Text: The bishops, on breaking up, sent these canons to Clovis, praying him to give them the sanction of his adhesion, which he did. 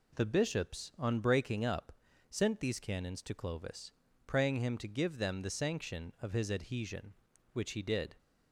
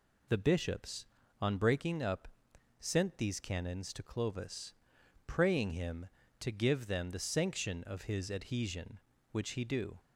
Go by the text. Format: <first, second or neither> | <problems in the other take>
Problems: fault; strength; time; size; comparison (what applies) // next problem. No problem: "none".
first | says "do" for "did"; at 9.6 s